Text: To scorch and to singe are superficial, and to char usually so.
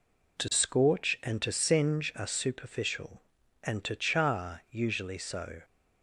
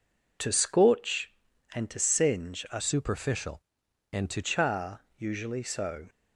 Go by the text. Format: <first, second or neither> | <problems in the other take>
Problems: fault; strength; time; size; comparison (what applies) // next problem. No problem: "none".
first | changes voice from "superficial" to "to"; from 2.7 to 4.4 s; 1.7 s long // pauses between "char" and "usually"; slight; at 5.0 s; 0.16 s long